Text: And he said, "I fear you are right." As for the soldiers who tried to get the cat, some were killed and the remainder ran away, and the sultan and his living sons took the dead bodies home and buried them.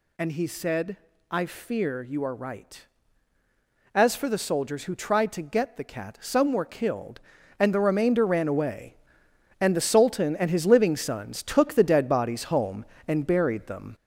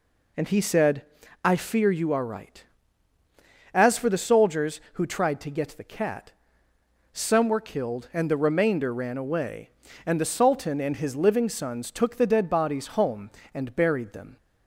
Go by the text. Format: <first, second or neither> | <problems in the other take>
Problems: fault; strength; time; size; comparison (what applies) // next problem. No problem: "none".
second | gets louder; noticeable; throughout; 4.5 dB